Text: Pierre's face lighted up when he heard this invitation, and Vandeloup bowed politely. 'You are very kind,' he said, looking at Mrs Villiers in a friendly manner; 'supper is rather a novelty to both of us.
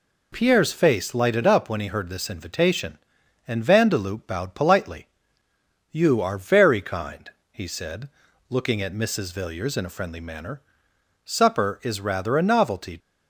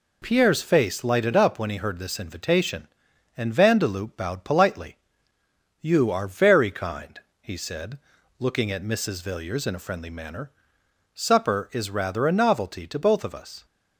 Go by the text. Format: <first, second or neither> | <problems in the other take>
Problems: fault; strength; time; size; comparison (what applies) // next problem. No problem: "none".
second | stops before "to both of us"; at 12.9 s